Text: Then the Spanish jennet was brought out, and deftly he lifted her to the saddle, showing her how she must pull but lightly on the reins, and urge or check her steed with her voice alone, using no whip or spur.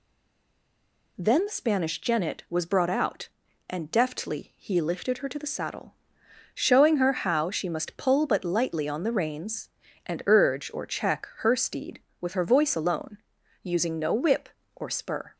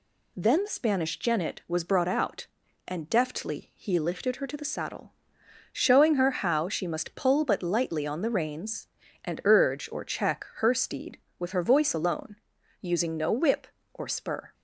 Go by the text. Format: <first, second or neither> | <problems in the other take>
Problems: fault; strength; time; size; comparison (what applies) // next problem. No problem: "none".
second | stays silent before the first word; until 1.1 s; 1.1 s long